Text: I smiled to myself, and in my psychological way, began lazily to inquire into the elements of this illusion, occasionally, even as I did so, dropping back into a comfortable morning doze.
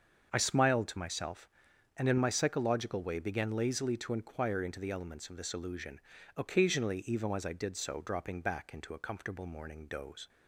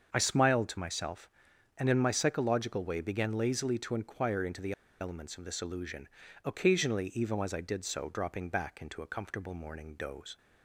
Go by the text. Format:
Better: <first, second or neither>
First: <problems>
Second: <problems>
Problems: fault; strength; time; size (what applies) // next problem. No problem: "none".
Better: first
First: starts louder than the rest; until 1.3 s; 6.5 dB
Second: starts louder than the rest; until 1.1 s; 6.5 dB // pauses between "the" and "elements"; slight; at 4.7 s; 0.28 s long